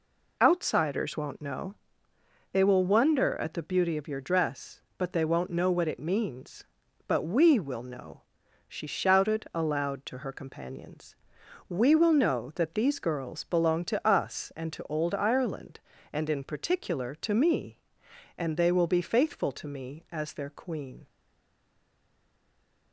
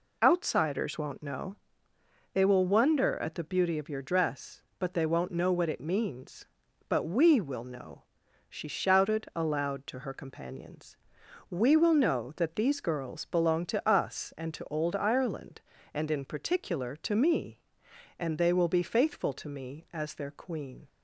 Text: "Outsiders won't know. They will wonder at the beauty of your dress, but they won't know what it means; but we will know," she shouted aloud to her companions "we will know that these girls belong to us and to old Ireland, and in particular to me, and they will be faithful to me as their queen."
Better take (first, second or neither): second